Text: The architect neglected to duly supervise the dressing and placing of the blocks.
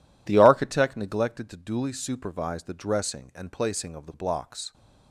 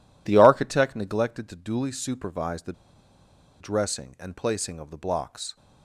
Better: first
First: none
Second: pauses between "the" and "dressing"; noticeable; at 2.7 s; 0.87 s long

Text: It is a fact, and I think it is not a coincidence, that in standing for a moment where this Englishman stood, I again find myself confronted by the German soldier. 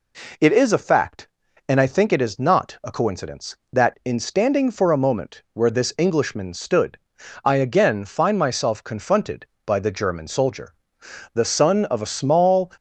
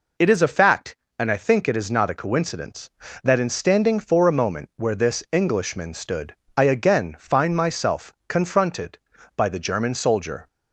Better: second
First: goes on to say "The son of a small"; from 11.3 s on; 1.3 s long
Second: none

